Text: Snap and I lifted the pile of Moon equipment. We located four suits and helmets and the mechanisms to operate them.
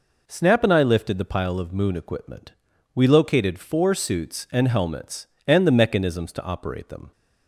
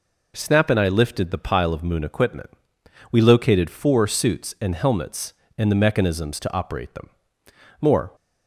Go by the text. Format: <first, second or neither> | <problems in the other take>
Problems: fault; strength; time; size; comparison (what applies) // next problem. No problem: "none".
first | goes on to say "More"; slight; from 7.8 s on; 0.34 s long